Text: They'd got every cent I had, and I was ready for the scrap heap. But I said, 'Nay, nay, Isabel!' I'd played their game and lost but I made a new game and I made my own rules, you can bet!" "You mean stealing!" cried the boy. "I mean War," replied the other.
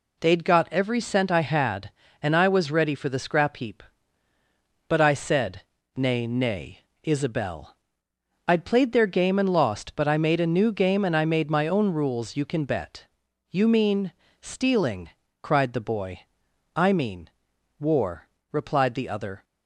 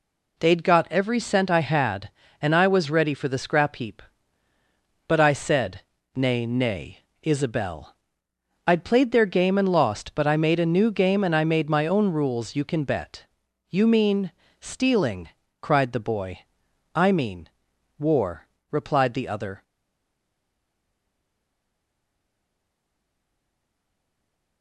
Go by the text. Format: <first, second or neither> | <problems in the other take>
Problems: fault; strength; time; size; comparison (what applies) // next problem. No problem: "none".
first | pauses between "mean" and "stealing"; slight; at 14.3 s; 0.30 s long; slight in the first // pauses between "mean" and "War"; noticeable; at 17.4 s; 0.48 s long; noticeable in the first // stays silent after the last word; strong; from 19.6 s on; 5.0 s long